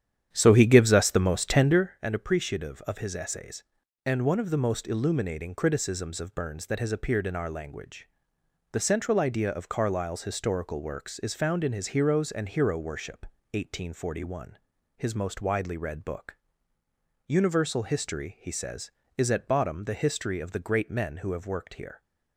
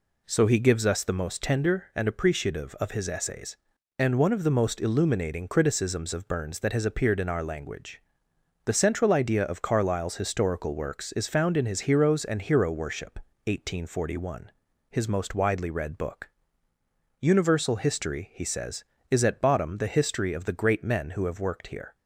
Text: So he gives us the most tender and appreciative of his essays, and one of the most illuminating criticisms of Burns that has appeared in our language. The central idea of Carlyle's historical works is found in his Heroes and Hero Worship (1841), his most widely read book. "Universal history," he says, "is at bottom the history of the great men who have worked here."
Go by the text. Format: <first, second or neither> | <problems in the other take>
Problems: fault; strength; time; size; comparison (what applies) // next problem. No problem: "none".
second | starts louder than the rest; strong; until 2.0 s; 9.5 dB